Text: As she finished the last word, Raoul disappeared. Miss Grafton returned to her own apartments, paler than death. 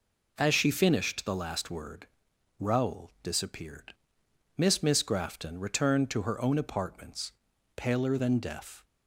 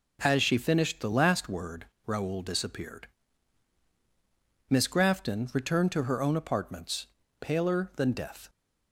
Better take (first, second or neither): second